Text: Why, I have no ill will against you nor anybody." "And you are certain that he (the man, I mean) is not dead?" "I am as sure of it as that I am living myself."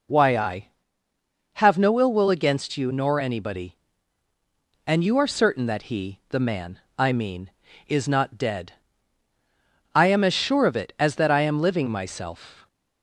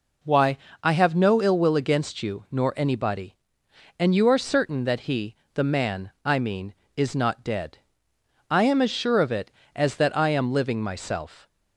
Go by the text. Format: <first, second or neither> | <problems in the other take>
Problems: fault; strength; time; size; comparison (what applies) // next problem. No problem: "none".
neither | none